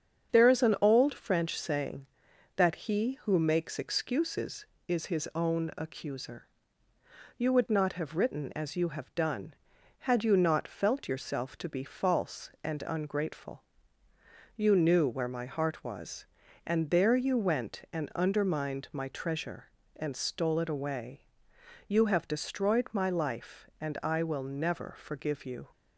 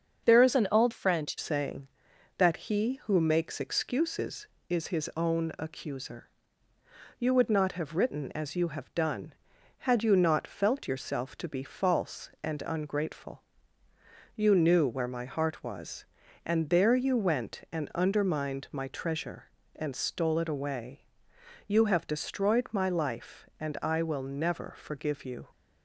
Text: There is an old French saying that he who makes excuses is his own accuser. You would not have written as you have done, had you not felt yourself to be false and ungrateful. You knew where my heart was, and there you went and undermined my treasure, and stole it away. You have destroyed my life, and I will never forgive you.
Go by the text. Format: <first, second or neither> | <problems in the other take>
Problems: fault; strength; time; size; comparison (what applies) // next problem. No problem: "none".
first | starts louder than the rest; until 1.3 s; 7 dB; strong in the first // changes voice from "an" to "French"; from 0.5 to 1.3 s; 0.8 s long